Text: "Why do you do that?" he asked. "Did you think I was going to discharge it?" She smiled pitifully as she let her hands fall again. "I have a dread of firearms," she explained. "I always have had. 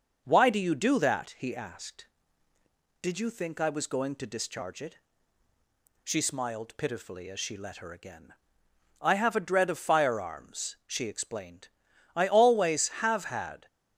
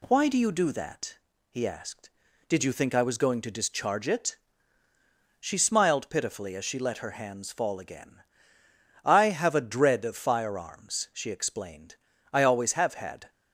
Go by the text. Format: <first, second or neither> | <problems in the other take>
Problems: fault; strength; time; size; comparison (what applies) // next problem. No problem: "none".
second | skips "hands fall"; at 7.9 s